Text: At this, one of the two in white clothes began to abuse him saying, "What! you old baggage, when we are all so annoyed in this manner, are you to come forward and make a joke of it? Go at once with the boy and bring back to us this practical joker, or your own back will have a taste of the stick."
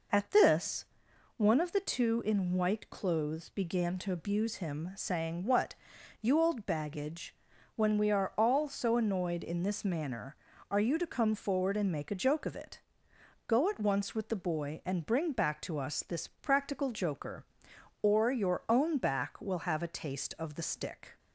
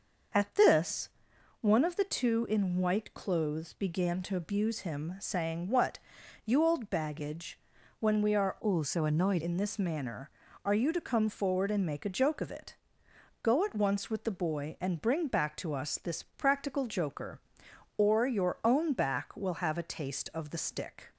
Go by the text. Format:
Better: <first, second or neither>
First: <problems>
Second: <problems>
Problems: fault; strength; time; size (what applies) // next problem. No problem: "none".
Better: first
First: none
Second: changes voice from "all" to "annoyed"; from 8.5 to 9.4 s; 0.9 s long